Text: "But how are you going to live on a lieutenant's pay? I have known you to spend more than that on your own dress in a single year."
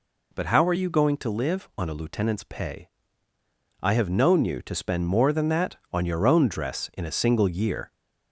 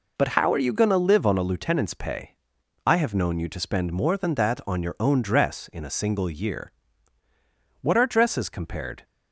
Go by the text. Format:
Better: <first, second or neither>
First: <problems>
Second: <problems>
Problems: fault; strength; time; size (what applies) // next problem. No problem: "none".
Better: first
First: none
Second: goes on to say "What are dresses compared"; noticeable; from 7.8 s on; 1.2 s long